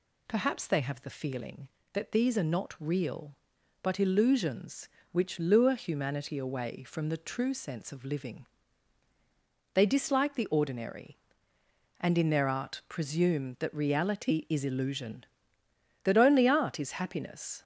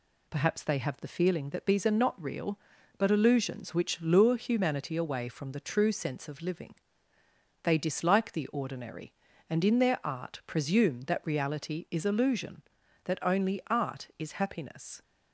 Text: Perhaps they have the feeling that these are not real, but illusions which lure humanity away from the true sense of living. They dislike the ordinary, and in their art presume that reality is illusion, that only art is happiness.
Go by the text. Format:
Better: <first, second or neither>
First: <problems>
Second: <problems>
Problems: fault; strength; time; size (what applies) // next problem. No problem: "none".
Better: neither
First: none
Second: none